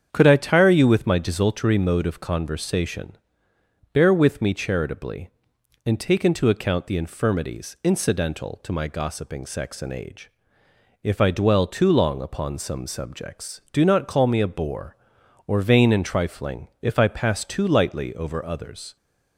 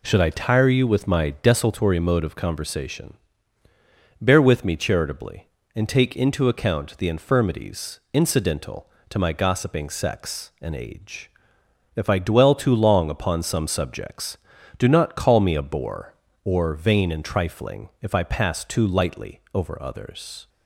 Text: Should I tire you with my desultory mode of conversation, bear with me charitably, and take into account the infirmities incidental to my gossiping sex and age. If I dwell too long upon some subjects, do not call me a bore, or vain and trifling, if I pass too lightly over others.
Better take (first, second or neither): second